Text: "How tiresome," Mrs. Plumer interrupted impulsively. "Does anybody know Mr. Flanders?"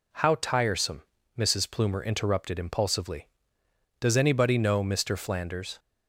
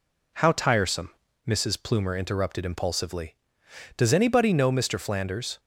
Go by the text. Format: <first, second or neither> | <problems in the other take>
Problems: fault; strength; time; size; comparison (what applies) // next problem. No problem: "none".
neither | none